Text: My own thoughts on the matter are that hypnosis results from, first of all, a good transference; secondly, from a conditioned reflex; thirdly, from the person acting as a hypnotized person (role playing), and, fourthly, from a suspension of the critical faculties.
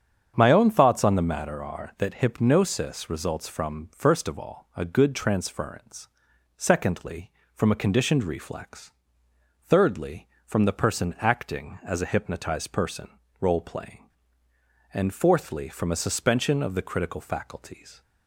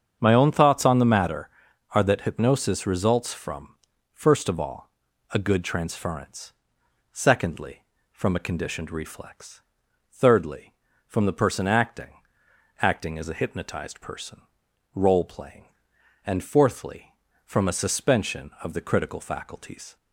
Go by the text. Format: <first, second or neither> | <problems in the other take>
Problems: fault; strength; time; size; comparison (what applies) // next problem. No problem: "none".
first | starts louder than the rest; strong; until 1.2 s; 7.5 dB; strong in the first // says "acting" twice; at 12.8 s